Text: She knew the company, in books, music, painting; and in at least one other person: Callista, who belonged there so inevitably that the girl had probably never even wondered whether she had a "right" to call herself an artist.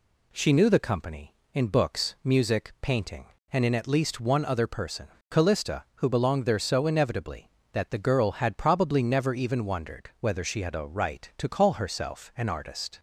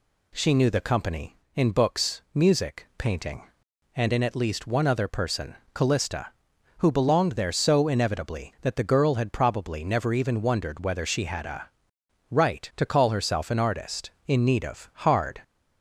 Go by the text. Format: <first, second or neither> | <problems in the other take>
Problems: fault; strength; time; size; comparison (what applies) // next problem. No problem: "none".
first | pauses between "a" and "right"; noticeable; at 11.6 s; 0.62 s long // goes on to say "In need of hard"; noticeable; from 14.2 s on; 1.1 s long